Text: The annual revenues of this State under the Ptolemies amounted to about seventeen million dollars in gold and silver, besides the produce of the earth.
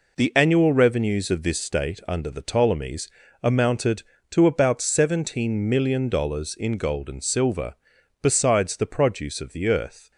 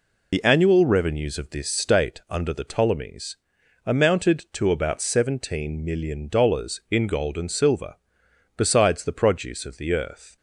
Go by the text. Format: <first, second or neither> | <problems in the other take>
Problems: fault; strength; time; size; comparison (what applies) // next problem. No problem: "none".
first | loses the start of "The"; at 0.3 s; 50 ms // pauses between "Ptolemies" and "amounted"; noticeable; at 3.3 s; 0.48 s long; slight in the first